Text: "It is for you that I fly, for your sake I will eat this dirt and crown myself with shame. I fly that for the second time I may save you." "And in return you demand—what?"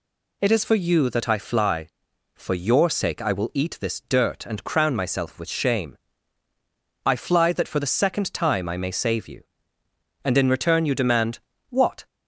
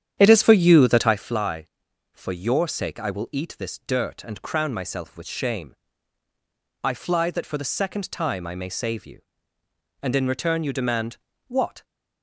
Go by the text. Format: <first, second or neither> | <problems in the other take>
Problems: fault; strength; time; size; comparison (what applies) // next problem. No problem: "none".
first | starts louder than the rest; strong; until 1.3 s; 9 dB